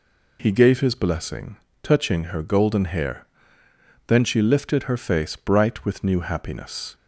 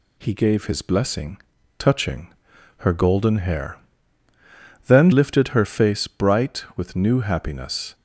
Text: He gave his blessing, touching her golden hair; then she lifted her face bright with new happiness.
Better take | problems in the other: first | pauses between "touching" and "her"; noticeable; at 2.3 s; 0.46 s long // skips "she"; at 5.1 s

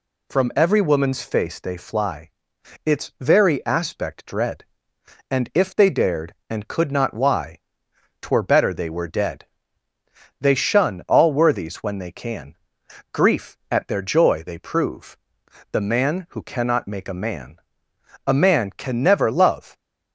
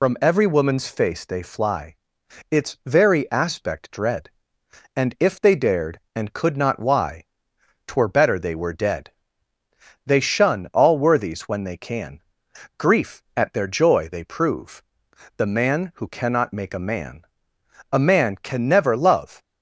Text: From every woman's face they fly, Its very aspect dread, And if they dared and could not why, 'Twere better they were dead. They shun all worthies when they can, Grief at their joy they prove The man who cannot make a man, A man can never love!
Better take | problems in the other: first | loses the start of "From"; at 0.0 s; 75 ms // pauses between "prove" and "The"; noticeable; at 14.8 s; 0.56 s long; noticeable in the first

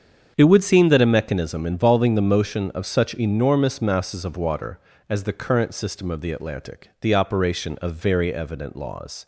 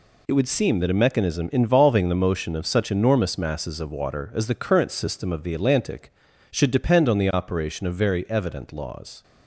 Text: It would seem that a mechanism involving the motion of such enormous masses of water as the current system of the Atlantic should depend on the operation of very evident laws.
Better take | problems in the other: second | starts louder than the rest; strong; until 1.3 s; 7.5 dB // skips "should depend on"; at 6.9 s

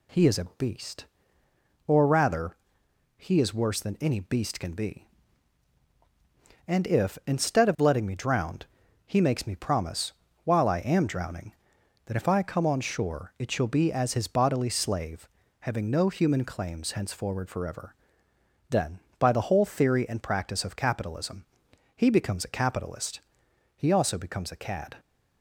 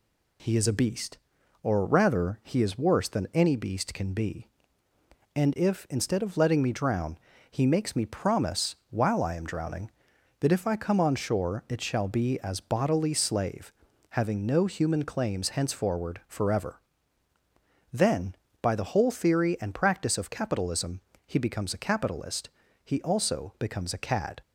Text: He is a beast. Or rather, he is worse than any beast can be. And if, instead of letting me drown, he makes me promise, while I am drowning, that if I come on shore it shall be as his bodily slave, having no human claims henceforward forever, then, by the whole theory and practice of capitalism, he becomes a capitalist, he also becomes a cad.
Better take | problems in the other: first | skips "his"; at 12.5 s

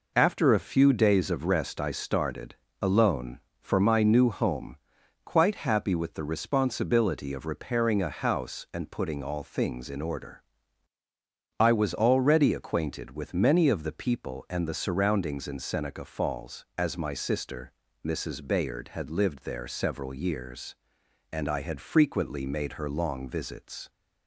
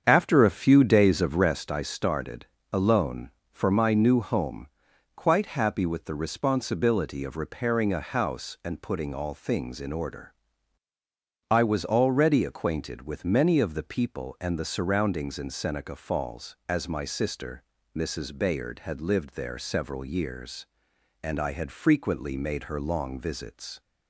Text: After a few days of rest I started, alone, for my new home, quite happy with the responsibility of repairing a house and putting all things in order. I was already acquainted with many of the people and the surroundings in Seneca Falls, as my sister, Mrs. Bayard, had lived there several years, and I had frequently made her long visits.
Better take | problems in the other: first | starts louder than the rest; strong; until 1.6 s; 7.5 dB

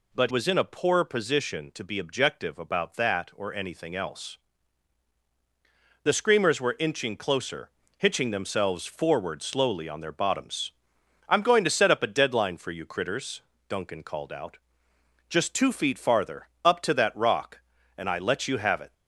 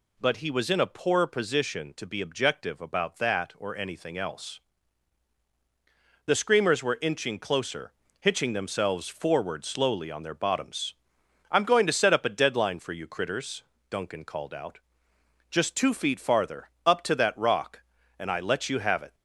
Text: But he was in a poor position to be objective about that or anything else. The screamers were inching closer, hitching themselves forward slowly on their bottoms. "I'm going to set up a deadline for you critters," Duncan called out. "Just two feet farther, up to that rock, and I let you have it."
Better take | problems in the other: second | skips "he"; at 0.3 s

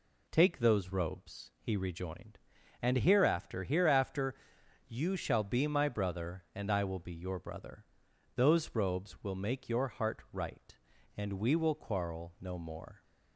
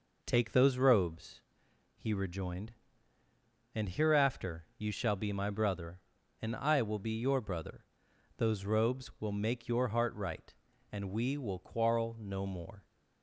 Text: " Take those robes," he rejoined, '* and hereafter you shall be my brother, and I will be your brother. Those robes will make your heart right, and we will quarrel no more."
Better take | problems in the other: second | says "hereafter" twice; at 3.6 s

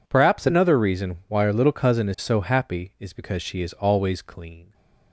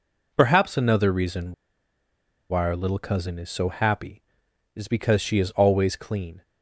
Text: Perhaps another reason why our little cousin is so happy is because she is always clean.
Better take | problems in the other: first | pauses between "reason" and "why"; noticeable; at 1.5 s; 0.97 s long

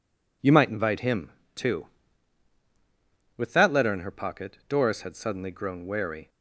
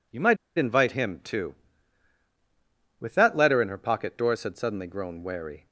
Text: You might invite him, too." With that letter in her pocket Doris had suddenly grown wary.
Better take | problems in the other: first | pauses between "might" and "invite"; slight; at 0.3 s; 0.21 s long

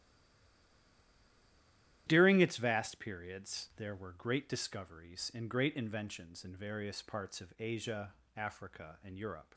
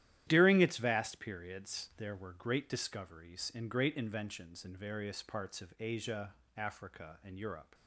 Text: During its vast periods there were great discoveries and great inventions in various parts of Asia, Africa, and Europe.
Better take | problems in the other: second | stays silent before the first word; noticeable; until 2.0 s; 2.0 s long // starts louder than the rest; strong; until 3.0 s; 12 dB; strong in the second

